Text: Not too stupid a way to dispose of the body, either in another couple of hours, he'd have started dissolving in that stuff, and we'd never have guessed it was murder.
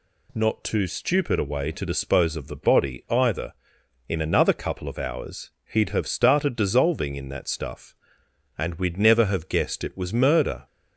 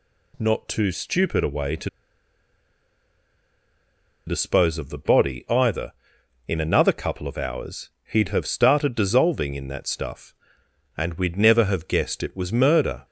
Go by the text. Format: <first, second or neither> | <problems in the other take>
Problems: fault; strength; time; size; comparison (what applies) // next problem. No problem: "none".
first | pauses between "to" and "dispose"; strong; at 1.8 s; 2.3 s long